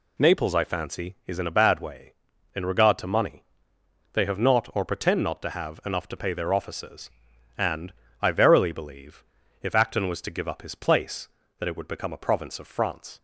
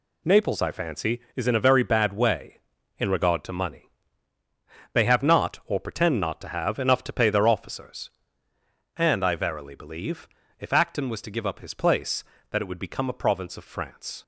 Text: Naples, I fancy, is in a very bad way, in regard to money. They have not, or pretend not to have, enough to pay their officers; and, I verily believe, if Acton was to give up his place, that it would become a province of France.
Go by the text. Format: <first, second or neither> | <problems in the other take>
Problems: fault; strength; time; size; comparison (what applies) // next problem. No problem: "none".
second | skips "very"; at 1.5 s